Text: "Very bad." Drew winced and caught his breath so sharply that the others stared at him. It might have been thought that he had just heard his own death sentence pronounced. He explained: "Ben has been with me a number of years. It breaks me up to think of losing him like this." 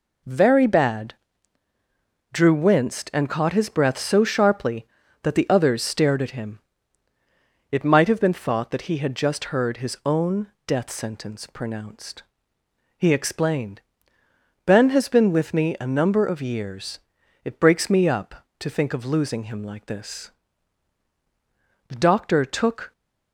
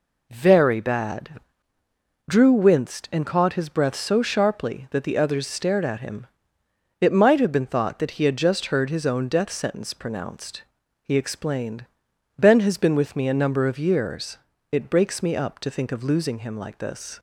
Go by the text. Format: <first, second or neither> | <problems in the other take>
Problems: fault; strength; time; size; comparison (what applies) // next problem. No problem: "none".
second | goes on to say "The doctor took"; noticeable; from 21.8 s on; 1.0 s long